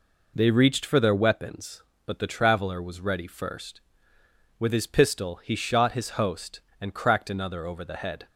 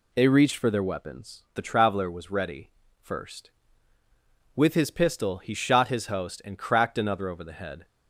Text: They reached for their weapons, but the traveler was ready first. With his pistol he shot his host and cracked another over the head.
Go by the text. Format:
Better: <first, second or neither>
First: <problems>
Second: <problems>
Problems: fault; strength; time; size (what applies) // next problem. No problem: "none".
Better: first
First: none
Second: skips "but"; at 1.4 s // pauses between "ready" and "first"; slight; at 2.7 s; 0.30 s long